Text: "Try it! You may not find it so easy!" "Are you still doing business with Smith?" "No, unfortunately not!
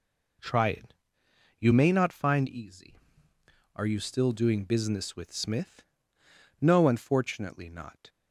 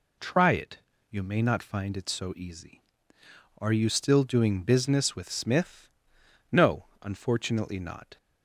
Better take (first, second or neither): second